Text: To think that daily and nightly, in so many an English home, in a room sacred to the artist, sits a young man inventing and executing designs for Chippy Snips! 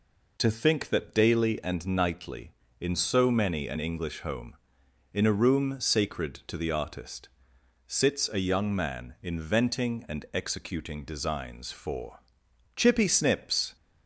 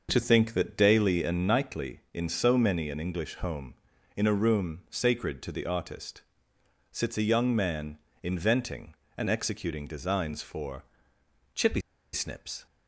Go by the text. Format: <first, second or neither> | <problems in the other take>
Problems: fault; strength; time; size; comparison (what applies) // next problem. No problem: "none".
first | starts louder than the rest; noticeable; until 1.1 s; 6 dB // pauses between "man" and "inventing"; slight; at 7.9 s; 0.28 s long // pauses between "for" and "Chippy"; noticeable; at 10.8 s; 0.72 s long; noticeable in the first // pauses between "Chippy" and "Snips"; slight; at 11.8 s; 0.32 s long